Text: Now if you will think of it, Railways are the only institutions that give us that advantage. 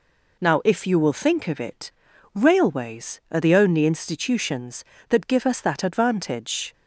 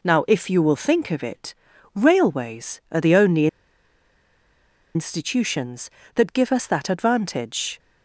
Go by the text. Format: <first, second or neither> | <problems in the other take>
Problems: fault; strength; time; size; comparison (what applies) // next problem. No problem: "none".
first | pauses between "only" and "institutions"; strong; at 3.4 s; 1.4 s long